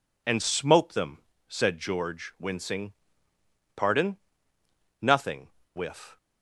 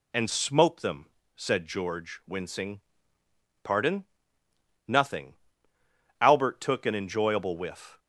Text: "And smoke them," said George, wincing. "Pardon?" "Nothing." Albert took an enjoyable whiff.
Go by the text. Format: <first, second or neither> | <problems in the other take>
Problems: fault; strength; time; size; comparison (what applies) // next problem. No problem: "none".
second | skips "Albert took an enjoyable"; at 5.6 s